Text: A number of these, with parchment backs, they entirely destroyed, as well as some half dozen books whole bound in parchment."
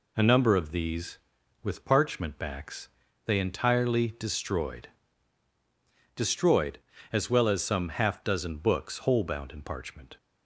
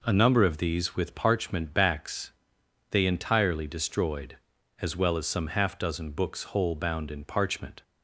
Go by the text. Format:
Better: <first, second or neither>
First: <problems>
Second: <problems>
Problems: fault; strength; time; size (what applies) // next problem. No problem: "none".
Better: second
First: says "destroyed" twice; at 6.1 s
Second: none